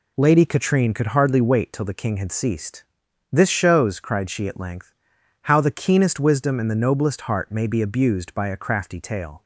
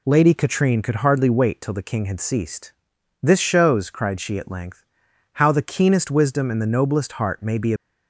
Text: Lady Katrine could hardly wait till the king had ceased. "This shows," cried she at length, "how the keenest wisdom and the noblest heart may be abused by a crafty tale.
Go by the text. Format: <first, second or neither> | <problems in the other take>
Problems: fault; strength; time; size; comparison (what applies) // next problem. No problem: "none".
first | stops before "abused by a crafty tale"; at 7.7 s